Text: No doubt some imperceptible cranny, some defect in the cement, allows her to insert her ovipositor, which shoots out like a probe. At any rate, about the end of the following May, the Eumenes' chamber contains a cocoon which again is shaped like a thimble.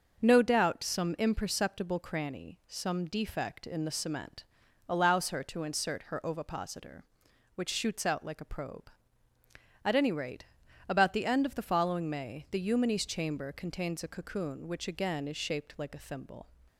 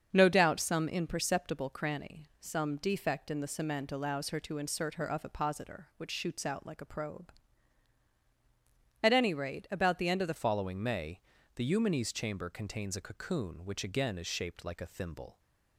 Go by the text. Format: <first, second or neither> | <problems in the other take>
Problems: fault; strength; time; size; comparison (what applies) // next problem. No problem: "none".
first | starts louder than the rest; until 1.1 s; 6.5 dB; noticeable in the first // changes voice at "following"; from 10.3 s on; 5.0 s long